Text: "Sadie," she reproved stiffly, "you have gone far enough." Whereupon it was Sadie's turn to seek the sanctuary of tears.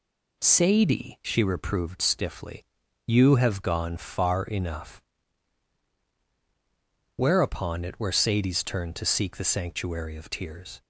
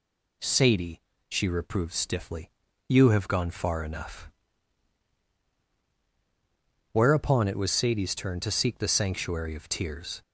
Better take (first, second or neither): second